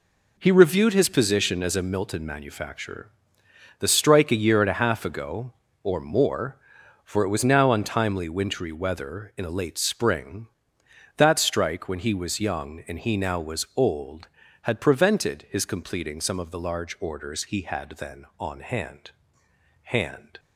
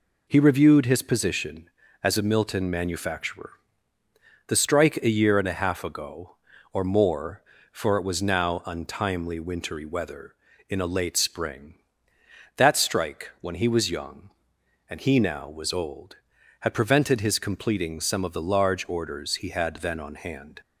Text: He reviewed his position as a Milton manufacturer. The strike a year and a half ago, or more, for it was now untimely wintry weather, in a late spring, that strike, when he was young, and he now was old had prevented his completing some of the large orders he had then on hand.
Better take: second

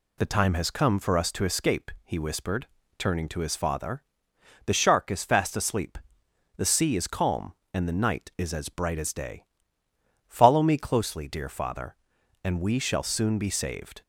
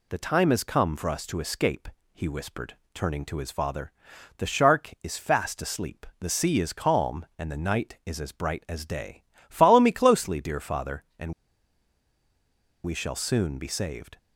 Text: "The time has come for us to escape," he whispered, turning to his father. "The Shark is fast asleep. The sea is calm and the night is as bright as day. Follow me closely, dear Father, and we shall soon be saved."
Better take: first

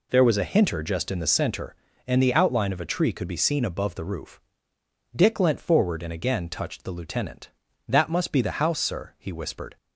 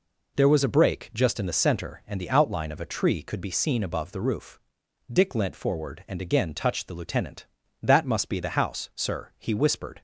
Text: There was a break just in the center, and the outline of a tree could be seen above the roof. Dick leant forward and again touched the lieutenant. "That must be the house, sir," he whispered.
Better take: second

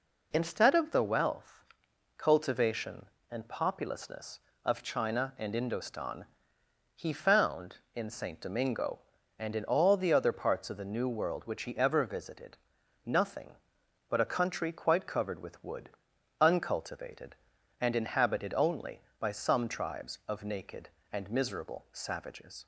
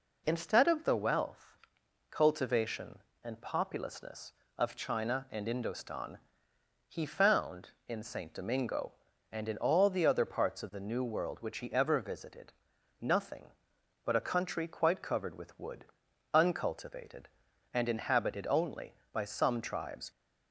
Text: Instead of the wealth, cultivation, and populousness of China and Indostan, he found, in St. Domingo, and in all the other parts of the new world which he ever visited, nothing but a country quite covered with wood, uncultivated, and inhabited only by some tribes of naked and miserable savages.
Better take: first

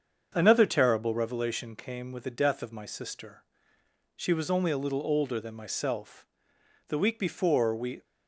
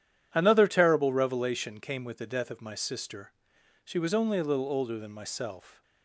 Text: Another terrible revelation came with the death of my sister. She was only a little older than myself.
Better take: second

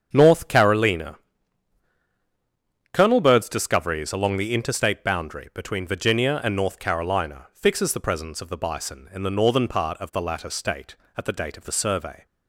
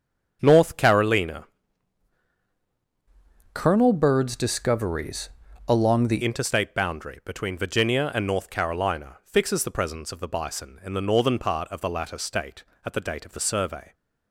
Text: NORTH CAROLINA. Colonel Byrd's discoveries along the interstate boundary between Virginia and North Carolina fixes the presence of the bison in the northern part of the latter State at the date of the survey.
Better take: first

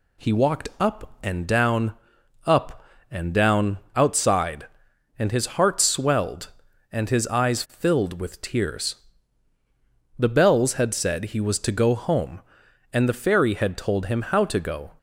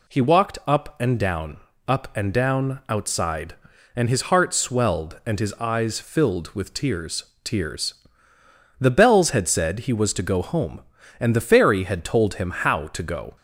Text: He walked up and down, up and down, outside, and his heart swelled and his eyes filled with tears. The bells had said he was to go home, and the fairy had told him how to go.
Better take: first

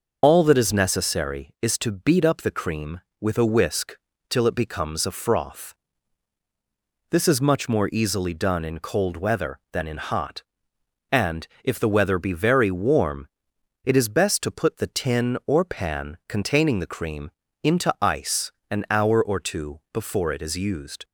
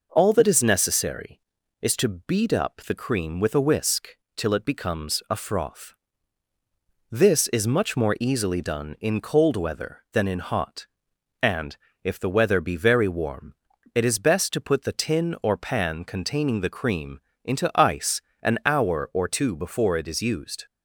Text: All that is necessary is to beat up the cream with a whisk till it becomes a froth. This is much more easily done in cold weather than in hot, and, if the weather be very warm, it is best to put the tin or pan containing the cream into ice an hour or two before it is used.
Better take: second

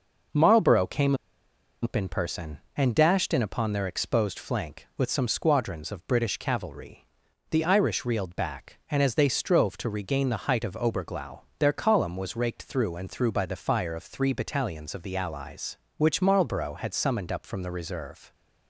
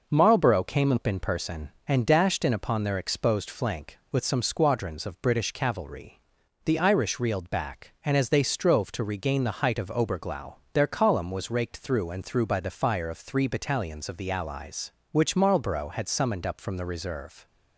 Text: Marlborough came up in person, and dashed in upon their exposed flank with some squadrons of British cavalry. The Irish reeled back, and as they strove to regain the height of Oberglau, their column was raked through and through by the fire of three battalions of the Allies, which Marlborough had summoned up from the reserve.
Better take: second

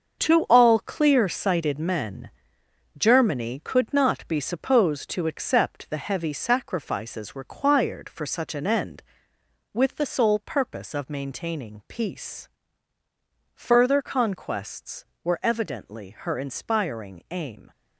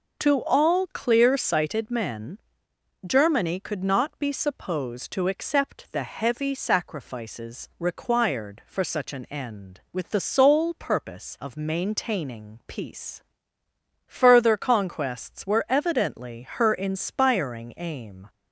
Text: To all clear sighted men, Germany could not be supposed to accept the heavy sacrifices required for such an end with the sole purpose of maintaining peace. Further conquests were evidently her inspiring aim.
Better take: second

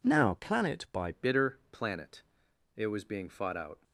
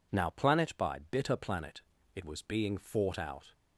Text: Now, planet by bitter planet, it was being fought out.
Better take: second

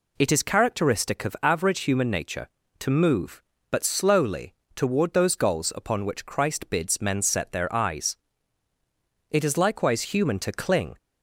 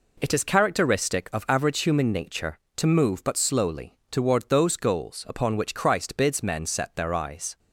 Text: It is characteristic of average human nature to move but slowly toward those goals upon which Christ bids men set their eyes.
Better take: second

